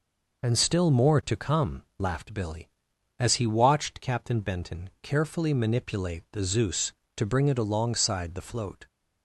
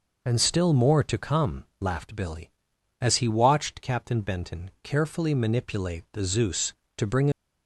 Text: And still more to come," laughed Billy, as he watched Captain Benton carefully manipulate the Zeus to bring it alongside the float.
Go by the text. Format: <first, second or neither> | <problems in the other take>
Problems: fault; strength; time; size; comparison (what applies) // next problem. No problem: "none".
first | stops before "it alongside the float"; at 7.3 s